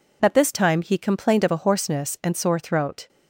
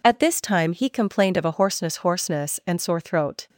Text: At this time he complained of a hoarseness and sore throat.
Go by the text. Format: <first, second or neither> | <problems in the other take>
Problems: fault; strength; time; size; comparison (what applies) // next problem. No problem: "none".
first | says "hoarseness" twice; at 1.9 s